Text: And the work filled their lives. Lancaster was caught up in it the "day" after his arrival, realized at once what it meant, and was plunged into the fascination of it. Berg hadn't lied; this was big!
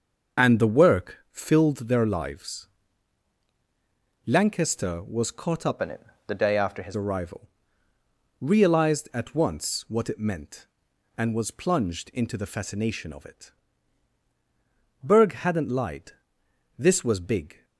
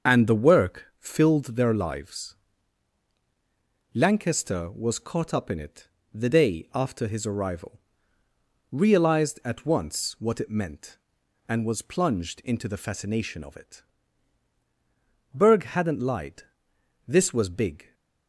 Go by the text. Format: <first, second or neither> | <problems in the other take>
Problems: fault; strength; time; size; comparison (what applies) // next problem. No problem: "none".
second | starts louder than the rest; until 1.4 s; 6.5 dB; also in the second // changes voice from "in" to "his"; from 5.8 to 6.9 s; 1.1 s long // pauses between "it" and "the"; slight; at 6.0 s; 0.26 s long; slight in the second